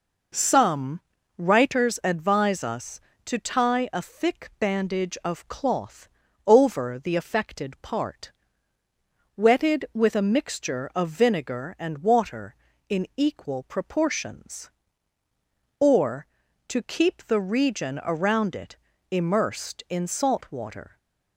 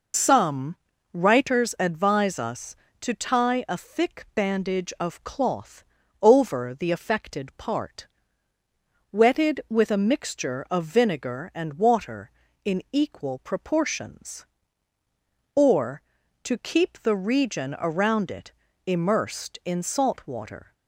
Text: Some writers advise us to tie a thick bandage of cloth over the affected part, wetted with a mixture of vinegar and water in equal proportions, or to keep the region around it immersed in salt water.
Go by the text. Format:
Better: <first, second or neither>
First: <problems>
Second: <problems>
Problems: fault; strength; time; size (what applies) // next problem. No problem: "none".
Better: first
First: pauses between "Some" and "writers"; at 0.9 s; 0.38 s long // pauses between "cloth" and "over"; at 6.0 s; 0.38 s long // pauses between "it" and "immersed"; slight; at 18.7 s; 0.36 s long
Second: loses the start of "Some"; at 0.1 s; 55 ms // pauses between "Some" and "writers"; at 0.7 s; 0.38 s long // pauses between "cloth" and "over"; at 5.8 s; 0.38 s long // pauses between "it" and "immersed"; slight; at 18.5 s; 0.36 s long